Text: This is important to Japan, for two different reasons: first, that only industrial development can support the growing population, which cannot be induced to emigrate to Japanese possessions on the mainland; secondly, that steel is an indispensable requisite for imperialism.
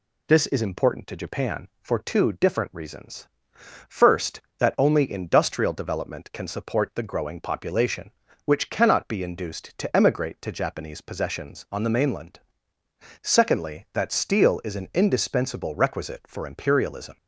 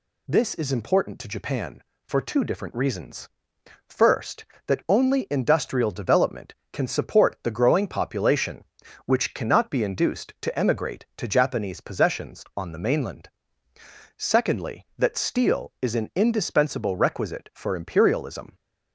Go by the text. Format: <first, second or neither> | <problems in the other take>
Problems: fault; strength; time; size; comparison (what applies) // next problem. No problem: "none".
neither | none